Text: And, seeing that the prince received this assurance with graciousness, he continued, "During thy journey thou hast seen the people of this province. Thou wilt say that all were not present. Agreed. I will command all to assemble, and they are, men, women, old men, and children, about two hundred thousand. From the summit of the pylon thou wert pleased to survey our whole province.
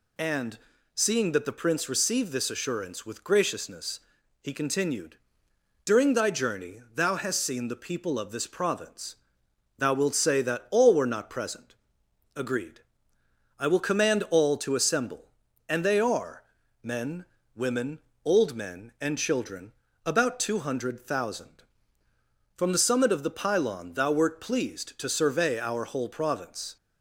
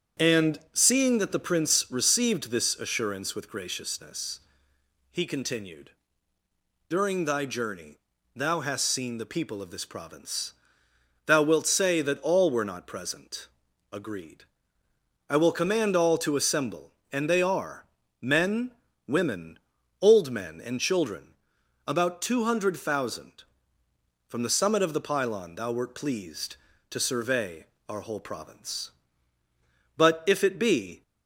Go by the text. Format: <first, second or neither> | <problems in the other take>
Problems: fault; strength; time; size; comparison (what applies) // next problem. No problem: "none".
first | starts louder than the rest; strong; until 1.3 s; 8 dB // pauses between "journey" and "thou"; slight; at 7.9 s; 0.36 s long // pauses between "survey" and "our"; slight; at 27.6 s; 0.22 s long // goes on to say "But if it be"; noticeable; from 29.9 s on; 1.0 s long